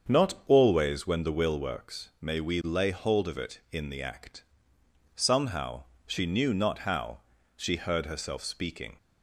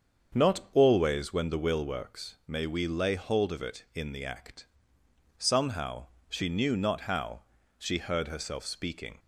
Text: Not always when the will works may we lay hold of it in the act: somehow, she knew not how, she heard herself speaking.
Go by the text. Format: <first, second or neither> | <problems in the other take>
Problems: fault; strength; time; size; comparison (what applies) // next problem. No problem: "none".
neither | starts louder than the rest; the same in both